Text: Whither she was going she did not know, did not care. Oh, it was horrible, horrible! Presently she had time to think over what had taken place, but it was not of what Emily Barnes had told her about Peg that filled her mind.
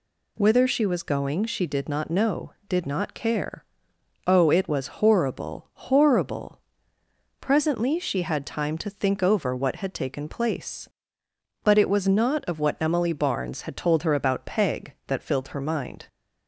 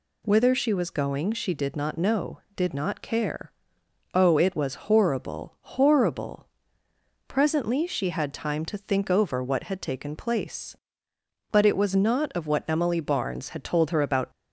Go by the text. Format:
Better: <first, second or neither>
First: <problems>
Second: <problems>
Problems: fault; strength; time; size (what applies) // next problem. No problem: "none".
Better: first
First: none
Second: stops before "Peg that filled her mind"; at 14.3 s